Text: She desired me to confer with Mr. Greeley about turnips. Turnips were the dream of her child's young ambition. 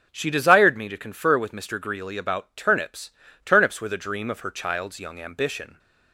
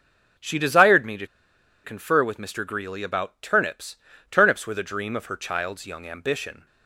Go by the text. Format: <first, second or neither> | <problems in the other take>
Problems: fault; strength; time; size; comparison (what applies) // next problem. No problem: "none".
first | pauses between "to" and "confer"; noticeable; at 1.2 s; 0.59 s long